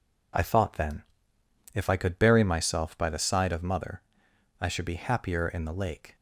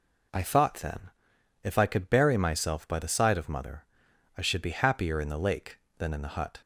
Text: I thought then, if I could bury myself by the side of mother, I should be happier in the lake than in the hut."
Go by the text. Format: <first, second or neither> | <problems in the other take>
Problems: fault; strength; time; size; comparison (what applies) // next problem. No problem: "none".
second | stops before "than in the hut"; at 6.1 s